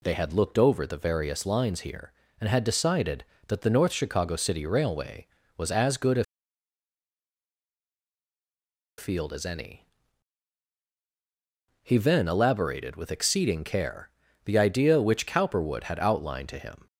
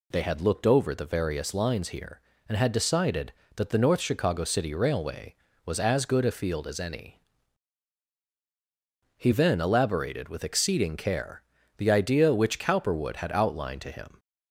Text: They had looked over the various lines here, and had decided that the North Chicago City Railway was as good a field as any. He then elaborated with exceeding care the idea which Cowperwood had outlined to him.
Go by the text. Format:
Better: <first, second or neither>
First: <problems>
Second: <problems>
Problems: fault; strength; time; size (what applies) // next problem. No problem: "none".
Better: second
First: pauses between "a" and "field"; strong; at 6.2 s; 2.7 s long // pauses between "care" and "the"; slight; at 14.1 s; 0.34 s long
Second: pauses between "care" and "the"; slight; at 11.4 s; 0.34 s long